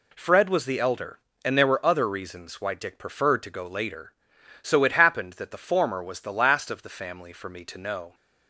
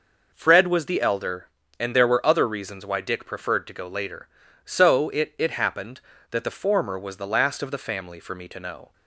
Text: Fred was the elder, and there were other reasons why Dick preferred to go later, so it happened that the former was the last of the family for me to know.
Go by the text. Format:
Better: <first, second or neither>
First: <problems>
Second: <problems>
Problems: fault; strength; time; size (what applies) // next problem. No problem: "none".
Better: first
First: none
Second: says "it" twice; at 5.3 s